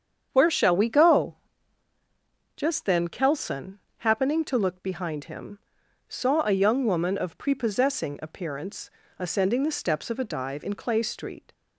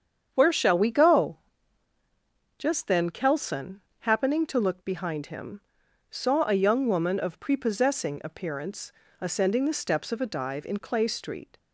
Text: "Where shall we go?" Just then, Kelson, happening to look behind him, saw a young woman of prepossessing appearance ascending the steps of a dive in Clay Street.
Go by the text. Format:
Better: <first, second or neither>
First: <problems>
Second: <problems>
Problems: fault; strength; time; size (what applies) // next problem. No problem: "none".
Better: neither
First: starts louder than the rest; strong; until 1.3 s; 8 dB // pauses between "appearance" and "ascending"; slight; at 8.8 s; 0.28 s long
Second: starts louder than the rest; strong; until 1.3 s; 8 dB // pauses between "appearance" and "ascending"; slight; at 8.9 s; 0.28 s long